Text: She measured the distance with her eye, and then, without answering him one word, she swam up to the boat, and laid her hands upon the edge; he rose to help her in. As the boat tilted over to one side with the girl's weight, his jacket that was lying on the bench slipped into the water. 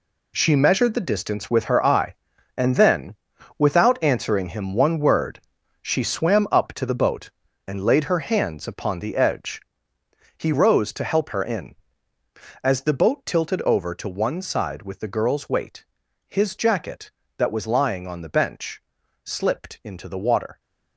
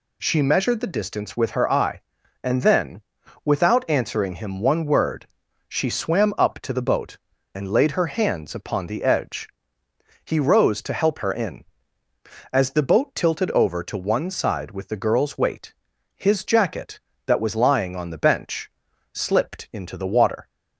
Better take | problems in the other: second | gets quieter; strong; throughout; 11 dB // pauses between "bench" and "slipped"; at 18.8 s; 0.44 s long; also in the second

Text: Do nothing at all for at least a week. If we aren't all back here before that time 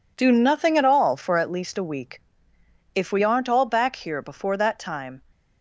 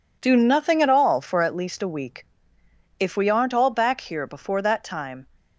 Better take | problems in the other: neither | none

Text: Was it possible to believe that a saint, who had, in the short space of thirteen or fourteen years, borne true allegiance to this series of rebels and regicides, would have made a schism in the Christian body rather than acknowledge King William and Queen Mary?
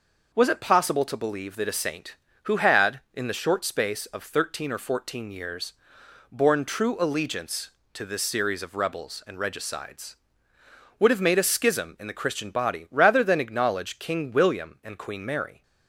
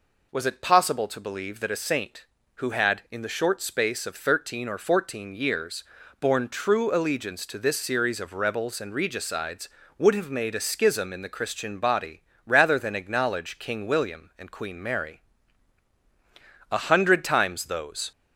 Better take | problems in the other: first | pauses between "body" and "rather"; slight; at 12.2 s; 0.24 s long // goes on to say "A hundred times those"; from 16.7 s on; 1.4 s long

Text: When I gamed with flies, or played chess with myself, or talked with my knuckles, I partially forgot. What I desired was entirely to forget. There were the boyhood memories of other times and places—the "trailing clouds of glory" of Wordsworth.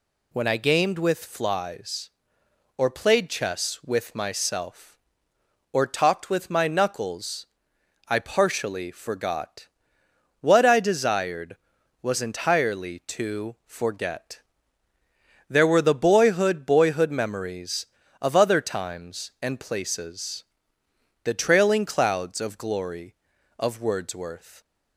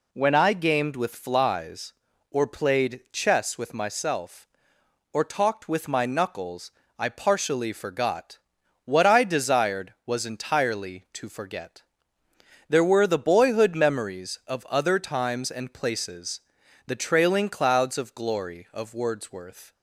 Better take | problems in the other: second | says "boyhood" twice; at 16.6 s

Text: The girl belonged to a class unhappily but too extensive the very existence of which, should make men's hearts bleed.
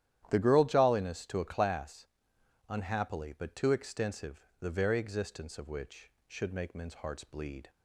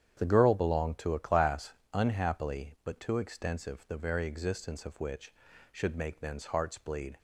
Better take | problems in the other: second | starts louder than the rest; strong; until 1.3 s; 11.5 dB; strong in the second // says "jolliness" for "belonged"; at 0.6 s // pauses between "class" and "unhappily"; noticeable; at 2.0 s; 0.64 s long; slight in the second // pauses between "extensive" and "the"; slight; at 4.3 s; 0.20 s long

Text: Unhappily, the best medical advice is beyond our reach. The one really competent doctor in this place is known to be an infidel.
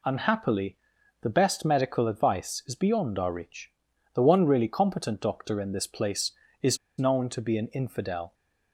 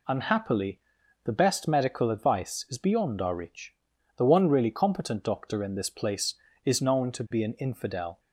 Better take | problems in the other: second | pauses between "is" and "known"; slight; at 6.7 s; 0.22 s long

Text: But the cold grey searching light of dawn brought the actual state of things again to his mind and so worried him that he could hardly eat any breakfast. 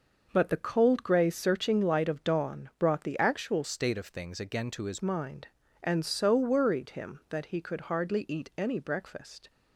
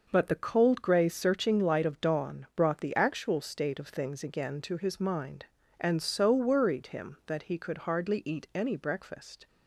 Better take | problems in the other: second | changes voice from "state" to "his"; from 3.6 to 4.9 s; 1.3 s long

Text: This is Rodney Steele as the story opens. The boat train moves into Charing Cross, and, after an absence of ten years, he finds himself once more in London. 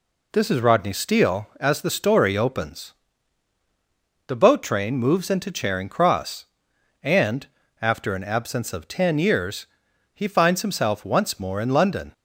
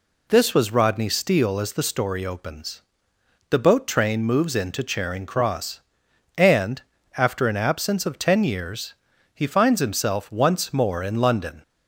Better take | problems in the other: first | says "was" for "is"; at 0.5 s

